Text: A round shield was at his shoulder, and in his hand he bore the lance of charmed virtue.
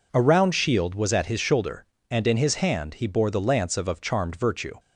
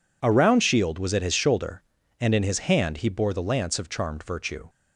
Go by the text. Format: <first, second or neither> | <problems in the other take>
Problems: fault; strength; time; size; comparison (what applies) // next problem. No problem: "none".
second | says "of" twice; at 3.8 s